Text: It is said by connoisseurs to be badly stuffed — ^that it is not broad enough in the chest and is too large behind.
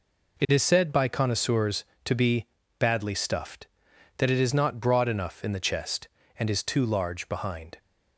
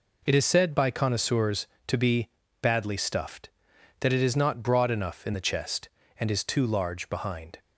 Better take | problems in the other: neither | pauses between "be" and "badly"; slight; the same in both

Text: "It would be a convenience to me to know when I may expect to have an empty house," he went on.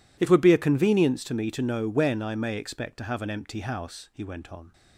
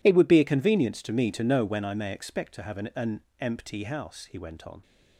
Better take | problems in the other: first | says "an" twice; at 2.9 s

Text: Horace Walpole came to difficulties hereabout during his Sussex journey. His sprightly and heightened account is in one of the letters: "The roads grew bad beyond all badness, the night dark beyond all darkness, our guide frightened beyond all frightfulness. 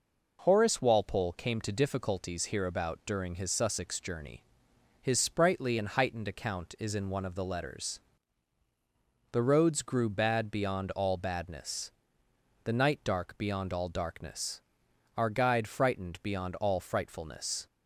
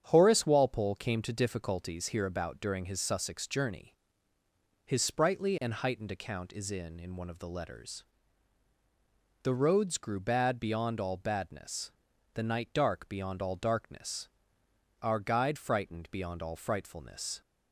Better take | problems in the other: first | starts louder than the rest; strong; until 1.0 s; 8.5 dB // says "in" twice; at 7.0 s

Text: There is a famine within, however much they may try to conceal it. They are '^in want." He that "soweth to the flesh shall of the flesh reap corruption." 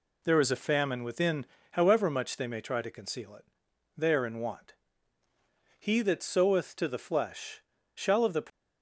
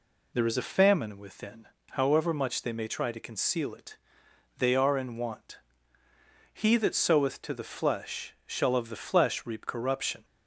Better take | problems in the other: second | pauses between "flesh" and "shall"; slight; at 7.6 s; 0.34 s long // stops before "flesh reap corruption"; at 8.5 s

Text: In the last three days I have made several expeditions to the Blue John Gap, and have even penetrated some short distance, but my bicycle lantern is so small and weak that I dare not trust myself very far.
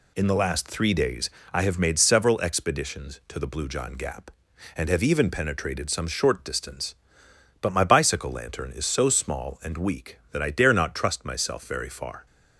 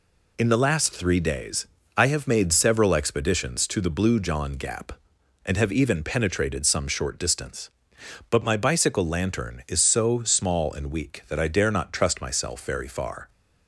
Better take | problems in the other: neither | pauses between "days" and "I"; slight; the same in both

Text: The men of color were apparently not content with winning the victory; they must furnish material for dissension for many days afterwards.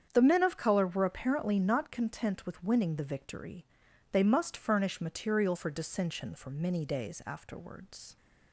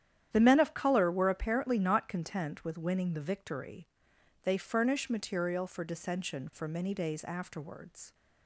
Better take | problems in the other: first | starts louder than the rest; strong; until 1.3 s; 10 dB; strong in the first // skips "must"; at 4.5 s

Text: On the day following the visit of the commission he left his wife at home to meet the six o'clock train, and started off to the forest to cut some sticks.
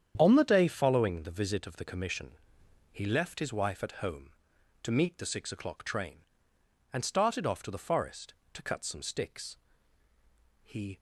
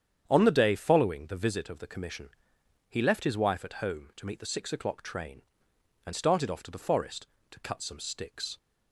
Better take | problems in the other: second | starts louder than the rest; strong; until 1.1 s; 8.5 dB; strong in the second // pauses between "commission" and "he"; noticeable; at 2.3 s; 0.62 s long; noticeable in the second // goes on to say "He"; slight; from 10.6 s on; 0.36 s long

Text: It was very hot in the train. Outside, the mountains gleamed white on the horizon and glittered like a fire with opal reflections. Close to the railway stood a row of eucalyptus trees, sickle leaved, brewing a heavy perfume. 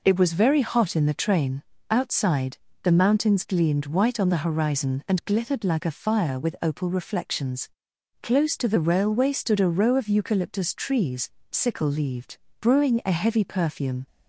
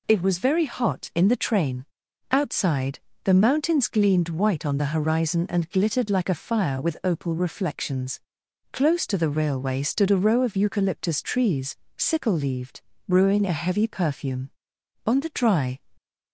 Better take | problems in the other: first | goes on to say "On the dry"; noticeable; from 15.0 s on; 0.74 s long

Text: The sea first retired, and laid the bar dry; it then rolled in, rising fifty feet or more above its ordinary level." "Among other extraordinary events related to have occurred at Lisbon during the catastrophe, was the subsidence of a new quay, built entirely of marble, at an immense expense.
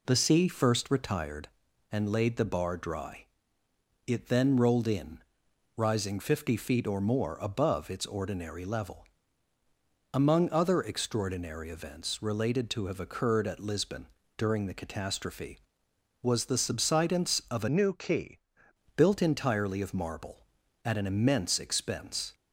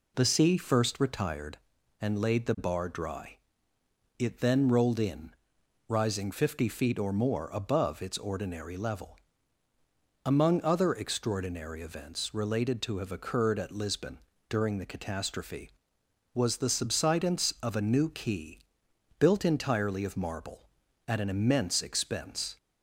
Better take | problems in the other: second | pauses between "Lisbon" and "during"; slight; at 14.0 s; 0.32 s long; slight in the second // changes voice from "new" to "quay"; from 17.6 to 18.4 s; 0.8 s long

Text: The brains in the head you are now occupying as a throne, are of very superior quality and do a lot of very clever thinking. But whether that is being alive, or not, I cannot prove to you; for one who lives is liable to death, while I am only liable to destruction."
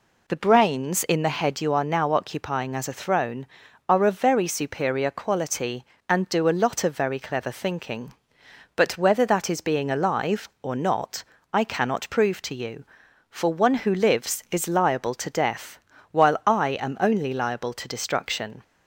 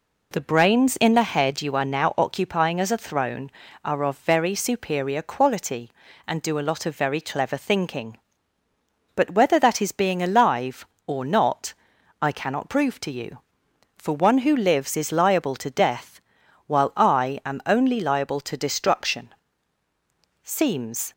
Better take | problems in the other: first | goes on to say "Seems"; noticeable; from 20.4 s on; 0.68 s long

